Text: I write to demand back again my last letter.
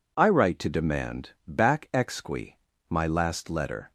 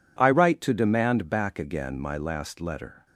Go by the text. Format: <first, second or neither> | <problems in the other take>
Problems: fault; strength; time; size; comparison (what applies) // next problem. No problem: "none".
second | pauses between "demand" and "back"; slight; at 1.2 s; 0.17 s long // says "exqui" for "again"; at 1.9 s